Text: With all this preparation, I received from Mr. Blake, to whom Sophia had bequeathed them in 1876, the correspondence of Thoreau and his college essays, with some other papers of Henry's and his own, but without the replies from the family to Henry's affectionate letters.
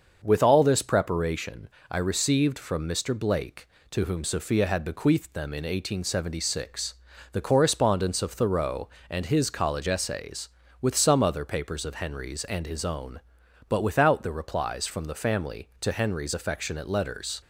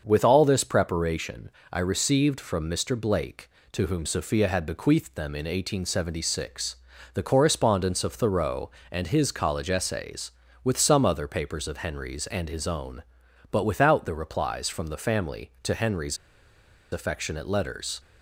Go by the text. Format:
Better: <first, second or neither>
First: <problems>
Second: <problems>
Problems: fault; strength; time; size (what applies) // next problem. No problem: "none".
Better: first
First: starts louder than the rest; until 1.2 s; 6.5 dB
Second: starts louder than the rest; until 1.0 s; 6.5 dB // pauses between "Henry's" and "affectionate"; noticeable; at 16.1 s; 0.77 s long